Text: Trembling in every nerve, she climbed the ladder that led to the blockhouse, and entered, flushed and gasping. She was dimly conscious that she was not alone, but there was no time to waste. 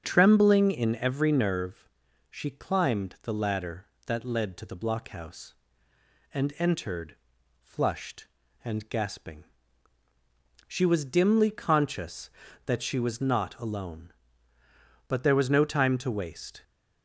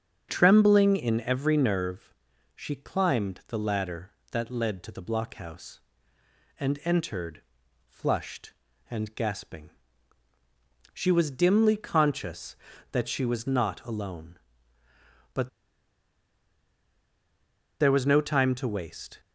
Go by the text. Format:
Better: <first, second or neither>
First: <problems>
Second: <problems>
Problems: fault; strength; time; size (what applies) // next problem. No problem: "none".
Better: first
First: starts louder than the rest; strong; until 1.0 s; 7 dB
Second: starts louder than the rest; strong; until 1.3 s; 7.5 dB // pauses between "but" and "there"; strong; at 15.4 s; 2.3 s long